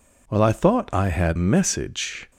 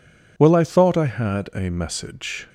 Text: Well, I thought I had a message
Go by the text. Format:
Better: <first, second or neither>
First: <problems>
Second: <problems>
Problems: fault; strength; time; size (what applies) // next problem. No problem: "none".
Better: second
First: skips "a"; at 1.3 s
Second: none